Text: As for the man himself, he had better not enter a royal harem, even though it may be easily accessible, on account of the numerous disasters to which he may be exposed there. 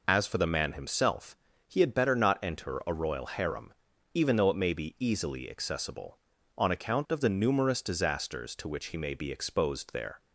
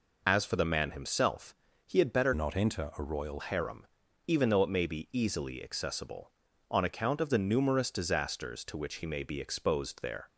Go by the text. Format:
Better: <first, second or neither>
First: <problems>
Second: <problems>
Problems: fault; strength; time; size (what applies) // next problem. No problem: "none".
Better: first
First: none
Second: changes voice from "not" to "royal"; from 2.3 to 3.4 s; 1.1 s long